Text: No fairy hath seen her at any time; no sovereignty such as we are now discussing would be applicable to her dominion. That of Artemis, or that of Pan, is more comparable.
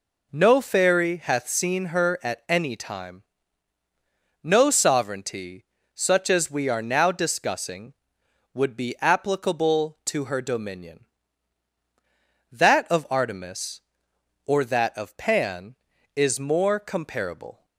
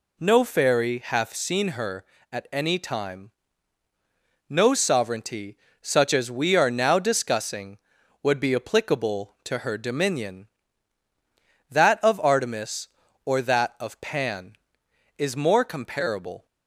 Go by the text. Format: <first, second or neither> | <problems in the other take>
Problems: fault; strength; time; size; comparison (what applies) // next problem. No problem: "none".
neither | pauses between "sovereignty" and "such"; slight; the same in both